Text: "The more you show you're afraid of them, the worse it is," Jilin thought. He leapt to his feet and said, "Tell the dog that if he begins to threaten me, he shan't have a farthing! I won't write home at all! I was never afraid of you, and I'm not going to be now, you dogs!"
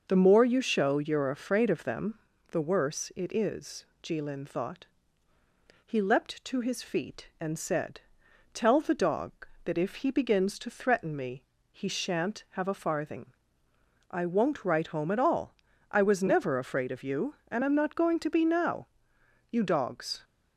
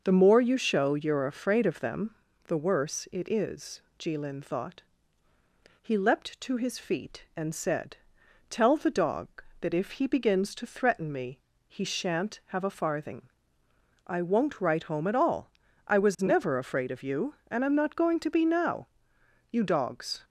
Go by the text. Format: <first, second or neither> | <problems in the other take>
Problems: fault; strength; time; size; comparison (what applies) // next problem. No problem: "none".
neither | none